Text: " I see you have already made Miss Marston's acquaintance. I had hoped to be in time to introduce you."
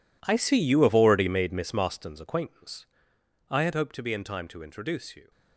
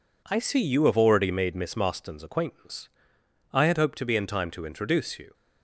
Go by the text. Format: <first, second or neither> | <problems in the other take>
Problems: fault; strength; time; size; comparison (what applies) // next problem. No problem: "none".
second | gets quieter; strong; throughout; 16 dB